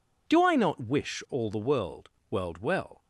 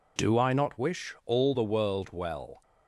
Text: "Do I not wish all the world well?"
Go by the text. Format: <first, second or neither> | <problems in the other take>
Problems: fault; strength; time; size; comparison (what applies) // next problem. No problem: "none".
second | says "world" twice; at 2.2 s